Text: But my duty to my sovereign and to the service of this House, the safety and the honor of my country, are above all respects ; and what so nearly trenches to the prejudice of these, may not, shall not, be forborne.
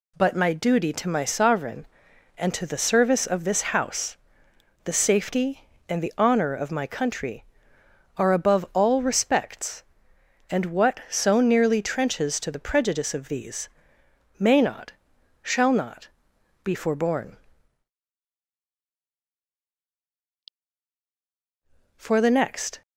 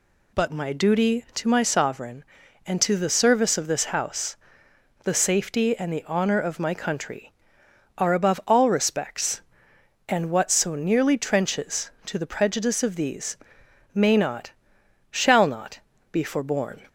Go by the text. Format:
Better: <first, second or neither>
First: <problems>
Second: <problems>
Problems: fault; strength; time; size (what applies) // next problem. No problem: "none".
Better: second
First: goes on to say "For the next"; noticeable; from 21.9 s on; 0.84 s long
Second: none